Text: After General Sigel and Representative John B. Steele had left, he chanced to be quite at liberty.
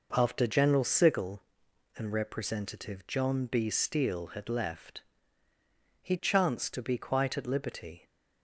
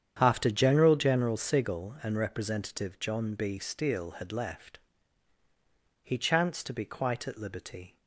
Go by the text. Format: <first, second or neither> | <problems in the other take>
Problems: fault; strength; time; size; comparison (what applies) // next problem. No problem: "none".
first | starts louder than the rest; strong; until 1.2 s; 8.5 dB // says "General" twice; at 0.9 s